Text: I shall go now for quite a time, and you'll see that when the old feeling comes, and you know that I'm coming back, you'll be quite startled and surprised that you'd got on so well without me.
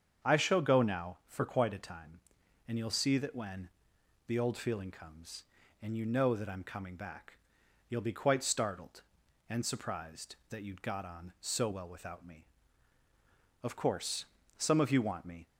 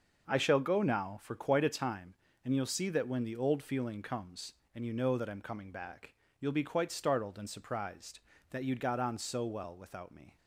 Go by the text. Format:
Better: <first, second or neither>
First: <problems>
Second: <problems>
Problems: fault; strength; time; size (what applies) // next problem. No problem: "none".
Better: second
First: starts louder than the rest; strong; until 1.3 s; 7.5 dB // pauses between "when" and "the"; noticeable; at 3.6 s; 0.58 s long // goes on to say "Of course some of you want me"; strong; from 13.6 s on; 1.8 s long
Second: starts louder than the rest; noticeable; until 1.3 s; 6 dB